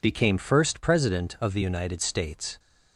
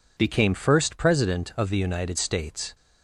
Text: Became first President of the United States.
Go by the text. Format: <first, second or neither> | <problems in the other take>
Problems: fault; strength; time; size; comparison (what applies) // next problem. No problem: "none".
neither | none